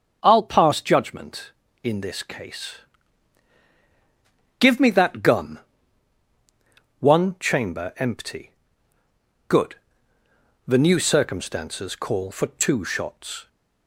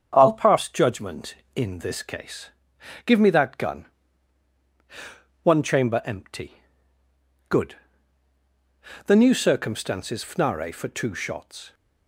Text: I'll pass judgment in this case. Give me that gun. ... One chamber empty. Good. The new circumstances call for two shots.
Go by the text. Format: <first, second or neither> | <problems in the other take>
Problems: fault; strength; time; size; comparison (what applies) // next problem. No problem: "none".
first | starts louder than the rest; strong; until 1.1 s; 7.5 dB; strong in the first // says "fnare" for "call"; at 10.2 s